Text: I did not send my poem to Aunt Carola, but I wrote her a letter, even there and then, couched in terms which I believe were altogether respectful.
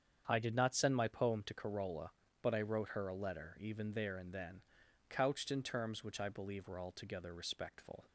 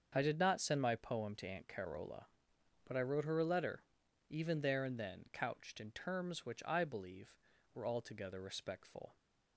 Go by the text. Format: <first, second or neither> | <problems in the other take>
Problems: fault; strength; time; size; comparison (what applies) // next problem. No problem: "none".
second | starts louder than the rest; strong; until 1.2 s; 7.5 dB; also in the second // skips "Aunt"; at 1.5 s